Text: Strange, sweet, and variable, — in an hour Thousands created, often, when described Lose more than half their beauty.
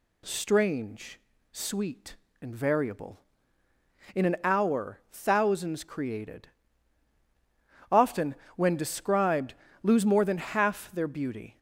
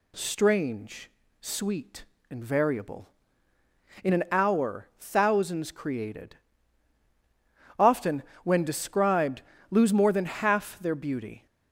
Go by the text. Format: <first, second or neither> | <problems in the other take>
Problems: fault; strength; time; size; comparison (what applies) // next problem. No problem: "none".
neither | pauses between "described" and "Lose"; slight; the same in both